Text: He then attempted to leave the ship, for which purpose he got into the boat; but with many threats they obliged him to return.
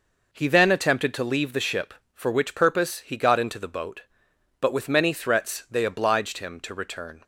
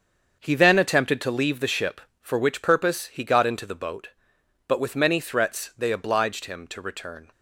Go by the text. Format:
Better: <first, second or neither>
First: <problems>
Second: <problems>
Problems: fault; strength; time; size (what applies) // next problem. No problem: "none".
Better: first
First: none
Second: gets quieter; strong; throughout; 8.5 dB